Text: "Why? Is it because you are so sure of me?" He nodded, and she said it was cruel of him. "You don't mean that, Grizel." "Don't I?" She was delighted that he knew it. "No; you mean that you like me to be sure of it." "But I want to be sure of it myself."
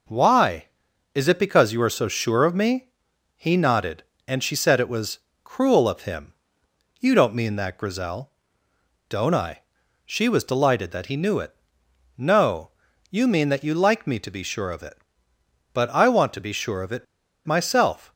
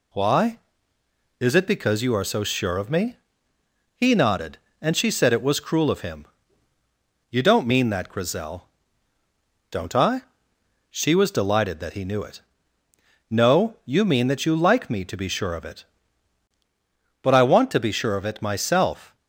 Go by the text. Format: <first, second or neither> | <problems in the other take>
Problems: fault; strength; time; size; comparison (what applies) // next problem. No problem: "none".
second | pauses between "was" and "cruel"; slight; at 5.1 s; 0.24 s long // pauses between "it" and "myself"; at 17.0 s; 0.40 s long